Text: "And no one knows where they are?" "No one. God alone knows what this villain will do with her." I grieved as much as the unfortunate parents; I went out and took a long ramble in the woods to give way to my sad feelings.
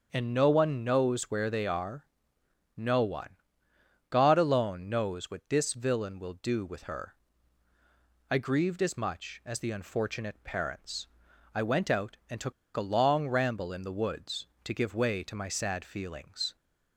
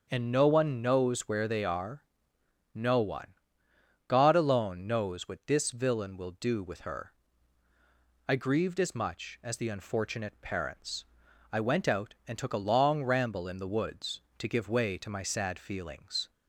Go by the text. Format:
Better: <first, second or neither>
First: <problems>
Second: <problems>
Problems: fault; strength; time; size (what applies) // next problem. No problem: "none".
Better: second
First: starts louder than the rest; until 1.1 s; 7 dB // pauses between "took" and "a"; slight; at 12.5 s; 0.24 s long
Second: starts louder than the rest; until 1.1 s; 7 dB